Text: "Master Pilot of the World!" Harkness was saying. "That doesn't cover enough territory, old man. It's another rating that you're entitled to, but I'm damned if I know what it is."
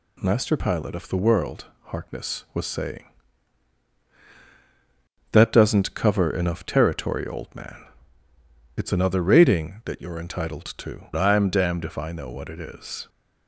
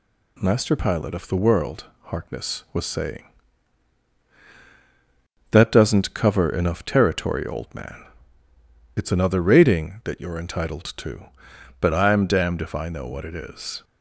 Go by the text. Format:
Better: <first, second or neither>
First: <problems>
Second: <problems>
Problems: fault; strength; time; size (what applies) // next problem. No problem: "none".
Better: second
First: skips "but"; at 11.1 s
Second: none